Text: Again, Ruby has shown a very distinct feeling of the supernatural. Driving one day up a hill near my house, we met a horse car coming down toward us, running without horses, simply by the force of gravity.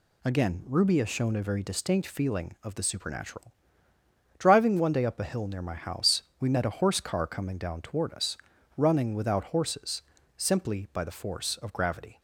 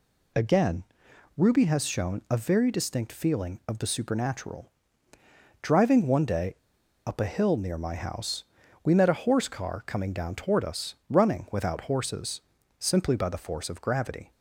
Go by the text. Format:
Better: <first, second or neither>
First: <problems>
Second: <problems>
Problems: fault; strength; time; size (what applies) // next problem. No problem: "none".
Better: first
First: none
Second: pauses between "day" and "up"; noticeable; at 6.5 s; 0.50 s long